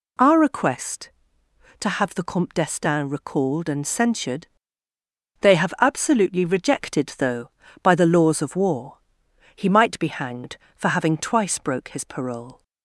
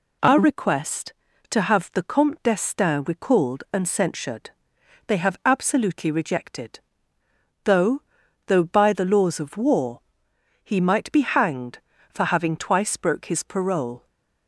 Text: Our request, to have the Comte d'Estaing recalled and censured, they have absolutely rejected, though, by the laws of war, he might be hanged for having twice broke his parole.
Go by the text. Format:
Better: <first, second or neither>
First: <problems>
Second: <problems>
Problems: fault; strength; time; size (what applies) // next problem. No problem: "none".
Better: first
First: none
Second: says "though" twice; at 8.4 s